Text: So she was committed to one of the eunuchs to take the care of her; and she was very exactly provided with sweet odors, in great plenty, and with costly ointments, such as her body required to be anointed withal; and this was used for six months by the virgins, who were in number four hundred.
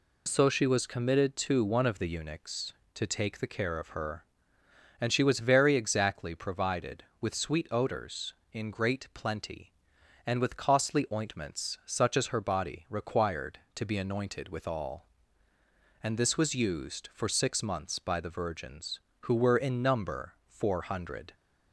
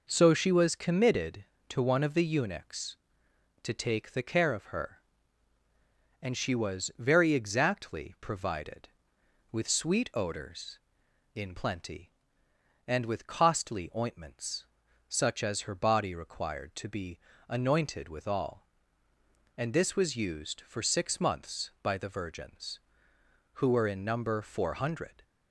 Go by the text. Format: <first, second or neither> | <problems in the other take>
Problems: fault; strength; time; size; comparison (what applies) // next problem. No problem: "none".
first | skips "great"; at 11.5 s // pauses between "be" and "anointed"; slight; at 17.1 s; 0.32 s long